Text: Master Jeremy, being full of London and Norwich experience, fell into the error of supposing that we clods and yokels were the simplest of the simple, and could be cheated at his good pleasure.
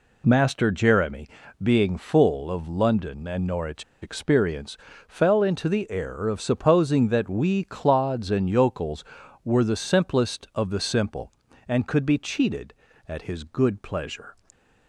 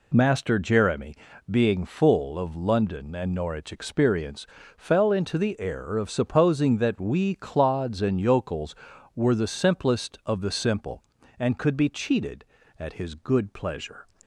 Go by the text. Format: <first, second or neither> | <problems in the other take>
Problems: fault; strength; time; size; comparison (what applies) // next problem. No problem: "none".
second | pauses between "Norwich" and "experience"; slight; at 3.8 s; 0.20 s long